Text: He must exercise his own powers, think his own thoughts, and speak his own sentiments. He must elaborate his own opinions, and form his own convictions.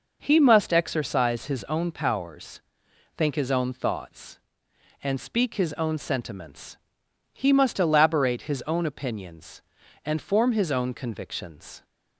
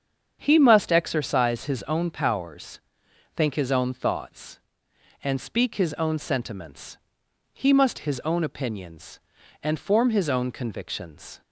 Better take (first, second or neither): first